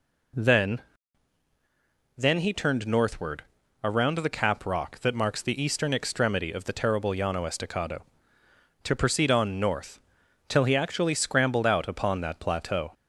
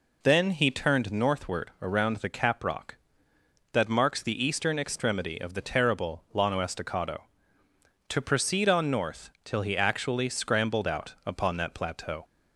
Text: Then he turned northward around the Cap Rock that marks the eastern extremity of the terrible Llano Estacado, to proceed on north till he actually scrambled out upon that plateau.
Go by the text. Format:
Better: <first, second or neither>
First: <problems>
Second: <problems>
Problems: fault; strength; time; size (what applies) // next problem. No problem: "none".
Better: second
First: says "Then" twice; at 2.1 s // pauses between "northward" and "around"; at 3.4 s; 0.40 s long // pauses between "north" and "till"; noticeable; at 10.0 s; 0.48 s long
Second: pauses between "north" and "till"; slight; at 9.2 s; 0.16 s long